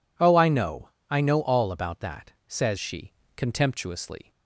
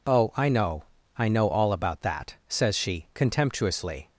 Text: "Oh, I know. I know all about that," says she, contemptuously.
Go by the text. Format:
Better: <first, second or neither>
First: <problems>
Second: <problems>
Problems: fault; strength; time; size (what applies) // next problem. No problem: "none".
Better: second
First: changes voice at "she"; from 2.7 s on; 1.5 s long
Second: none